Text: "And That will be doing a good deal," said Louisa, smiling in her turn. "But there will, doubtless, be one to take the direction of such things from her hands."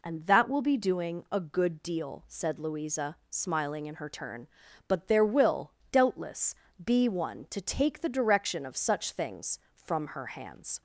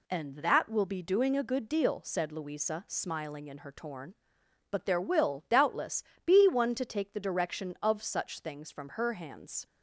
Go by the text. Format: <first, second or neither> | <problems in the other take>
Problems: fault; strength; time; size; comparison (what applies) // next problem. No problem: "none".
first | says "torn" for "turn"; at 3.7 s